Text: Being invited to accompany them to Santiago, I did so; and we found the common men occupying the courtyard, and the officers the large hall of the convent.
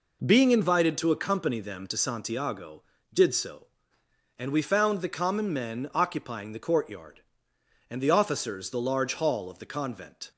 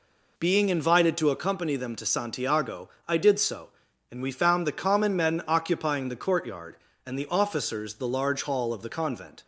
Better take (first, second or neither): second